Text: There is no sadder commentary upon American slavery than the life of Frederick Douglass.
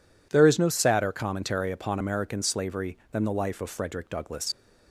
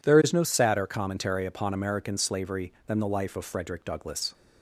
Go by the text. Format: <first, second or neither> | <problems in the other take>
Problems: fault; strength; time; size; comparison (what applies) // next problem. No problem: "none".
second | leaves "Douglass" unfinished; at 4.5 s; 55 ms